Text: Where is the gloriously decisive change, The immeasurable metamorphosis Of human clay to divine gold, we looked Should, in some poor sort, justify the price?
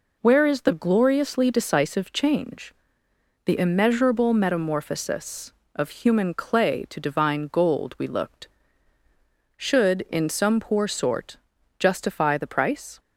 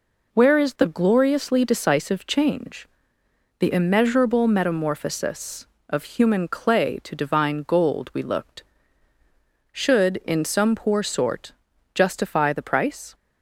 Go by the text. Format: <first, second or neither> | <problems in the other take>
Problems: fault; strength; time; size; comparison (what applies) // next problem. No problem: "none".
neither | none